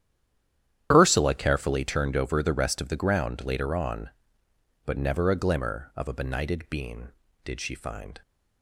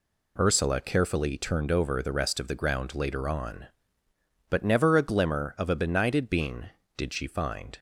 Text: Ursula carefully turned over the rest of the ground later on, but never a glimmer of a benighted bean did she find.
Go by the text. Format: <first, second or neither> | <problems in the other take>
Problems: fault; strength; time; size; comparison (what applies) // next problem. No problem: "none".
second | stays silent before the first word; slight; until 0.9 s; 0.9 s long // starts louder than the rest; strong; until 1.9 s; 10.5 dB